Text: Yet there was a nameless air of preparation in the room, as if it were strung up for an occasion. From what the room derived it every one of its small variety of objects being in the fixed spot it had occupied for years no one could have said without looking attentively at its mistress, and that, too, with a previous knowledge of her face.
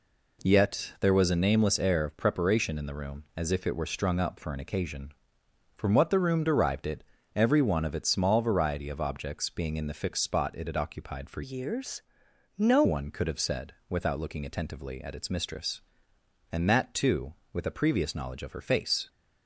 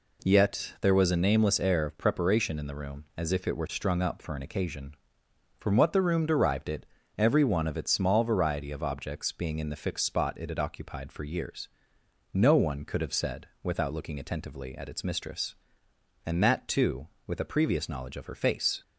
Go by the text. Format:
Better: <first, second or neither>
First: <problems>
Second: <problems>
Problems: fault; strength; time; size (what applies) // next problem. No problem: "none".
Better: second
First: pauses between "it" and "every"; slight; at 7.0 s; 0.32 s long // changes voice from "years" to "no"; from 11.4 to 12.8 s; 1.4 s long // pauses between "years" and "no"; noticeable; at 12.0 s; 0.56 s long // pauses between "said" and "without"; slight; at 13.7 s; 0.16 s long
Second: pauses between "it" and "every"; slight; at 6.8 s; 0.32 s long // pauses between "years" and "no"; noticeable; at 11.6 s; 0.64 s long // pauses between "said" and "without"; slight; at 13.4 s; 0.16 s long